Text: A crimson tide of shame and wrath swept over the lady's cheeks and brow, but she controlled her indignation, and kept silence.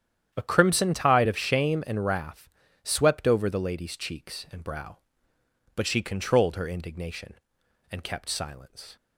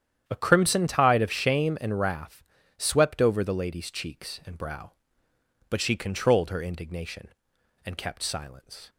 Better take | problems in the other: neither | starts louder than the rest; strong; the same in both // pauses between "wrath" and "swept"; slight; the same in both

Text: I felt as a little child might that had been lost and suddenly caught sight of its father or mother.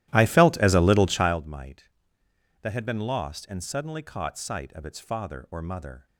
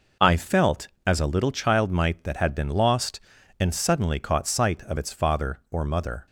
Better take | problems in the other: second | starts louder than the rest; strong; until 1.4 s; 14.5 dB

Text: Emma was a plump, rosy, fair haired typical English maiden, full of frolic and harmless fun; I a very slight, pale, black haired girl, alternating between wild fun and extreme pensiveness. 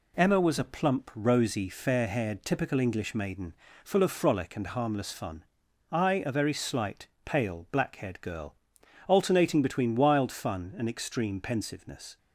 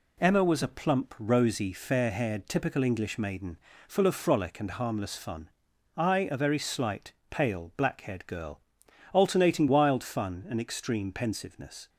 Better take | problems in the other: first | skips "between"; at 9.6 s

